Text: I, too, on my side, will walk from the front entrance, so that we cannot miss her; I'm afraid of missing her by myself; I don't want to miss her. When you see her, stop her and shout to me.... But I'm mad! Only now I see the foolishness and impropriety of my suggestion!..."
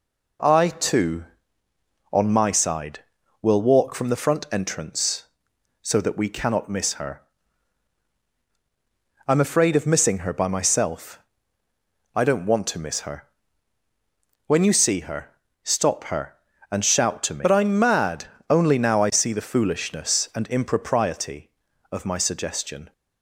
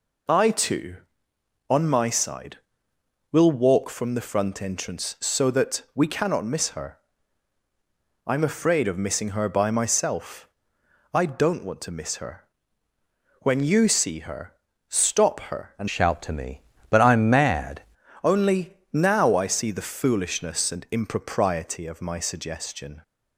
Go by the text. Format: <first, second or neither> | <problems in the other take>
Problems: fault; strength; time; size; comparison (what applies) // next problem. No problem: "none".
first | changes voice from "shout" to "mad"; from 15.8 to 17.8 s; 2.0 s long // pauses between "Only" and "now"; slight; at 18.7 s; 0.18 s long